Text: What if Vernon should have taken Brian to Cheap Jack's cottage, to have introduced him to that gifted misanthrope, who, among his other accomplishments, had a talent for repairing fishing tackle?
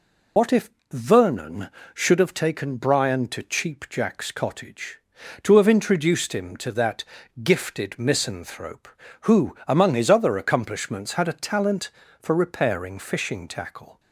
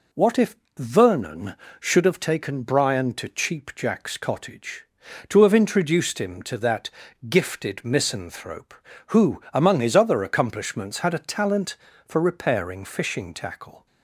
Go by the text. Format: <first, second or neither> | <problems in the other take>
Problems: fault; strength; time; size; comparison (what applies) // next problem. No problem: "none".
second | loses the start of "What"; at 0.3 s; 85 ms // pauses between "if" and "Vernon"; slight; at 0.6 s; 0.20 s long; slight in the second // pauses between "that" and "gifted"; at 7.0 s; 0.40 s long; also in the second